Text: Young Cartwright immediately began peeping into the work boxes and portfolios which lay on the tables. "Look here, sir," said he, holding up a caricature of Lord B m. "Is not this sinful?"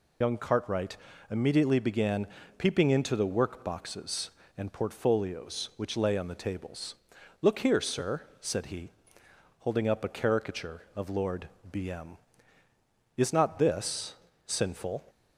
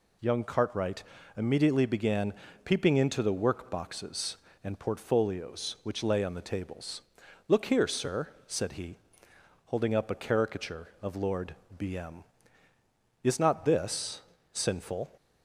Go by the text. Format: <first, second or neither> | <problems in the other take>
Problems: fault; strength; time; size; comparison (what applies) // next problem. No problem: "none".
second | loses the start of "Young"; at 0.2 s; 60 ms // pauses between "Cartwright" and "immediately"; slight; at 0.9 s; 0.34 s long; slight in the second // pauses between "began" and "peeping"; slight; at 2.2 s; 0.32 s long; slight in the second // pauses between "Lord" and "B"; slight; at 11.4 s; 0.22 s long; slight in the second // pauses between "this" and "sinful"; slight; at 14.1 s; 0.32 s long; slight in the second